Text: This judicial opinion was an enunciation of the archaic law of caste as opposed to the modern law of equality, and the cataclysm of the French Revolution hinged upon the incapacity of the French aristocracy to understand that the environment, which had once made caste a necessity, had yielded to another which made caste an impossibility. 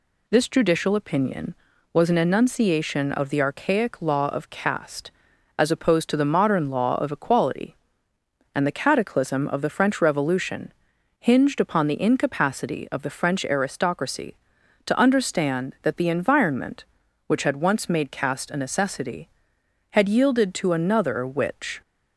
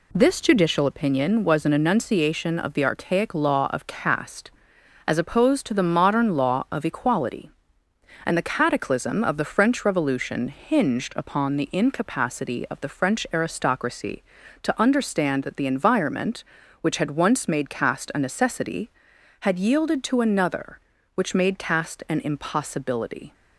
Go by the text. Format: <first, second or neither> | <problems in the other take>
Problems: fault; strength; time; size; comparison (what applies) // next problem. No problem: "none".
second | pauses between "Revolution" and "hinged"; noticeable; at 10.7 s; 0.48 s long // stops before "made caste an impossibility"; at 21.8 s